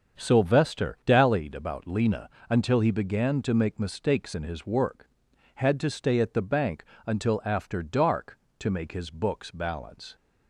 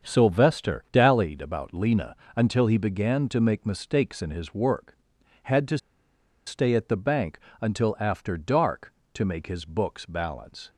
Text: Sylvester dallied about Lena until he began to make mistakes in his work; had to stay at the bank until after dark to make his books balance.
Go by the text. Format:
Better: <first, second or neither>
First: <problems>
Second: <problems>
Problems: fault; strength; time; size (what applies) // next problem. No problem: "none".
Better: first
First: starts louder than the rest; until 1.2 s; 7 dB // pauses between "Lena" and "until"; slight; at 2.2 s; 0.20 s long // pauses between "bank" and "until"; slight; at 6.8 s; 0.20 s long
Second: starts louder than the rest; until 1.1 s; 7 dB // pauses between "Lena" and "until"; slight; at 2.1 s; 0.20 s long // pauses between "to" and "stay"; noticeable; at 5.7 s; 0.69 s long // pauses between "bank" and "until"; slight; at 7.3 s; 0.20 s long